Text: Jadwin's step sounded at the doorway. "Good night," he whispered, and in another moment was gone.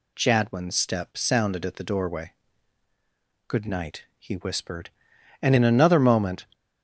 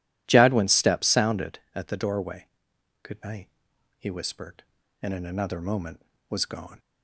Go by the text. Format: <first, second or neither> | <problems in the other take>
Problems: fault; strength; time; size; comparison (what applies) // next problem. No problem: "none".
second | stops before "was gone"; at 6.5 s